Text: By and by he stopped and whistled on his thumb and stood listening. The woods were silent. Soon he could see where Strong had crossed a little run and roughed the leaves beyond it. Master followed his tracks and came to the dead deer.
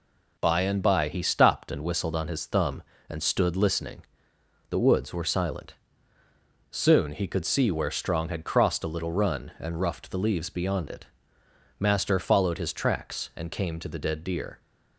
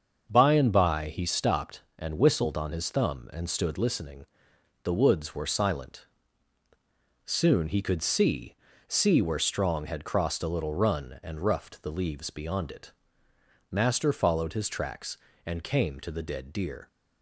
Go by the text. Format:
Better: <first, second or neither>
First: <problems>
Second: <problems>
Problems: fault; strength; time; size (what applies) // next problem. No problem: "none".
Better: first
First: none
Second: starts louder than the rest; until 1.3 s; 6.5 dB // says "see" twice; at 8.8 s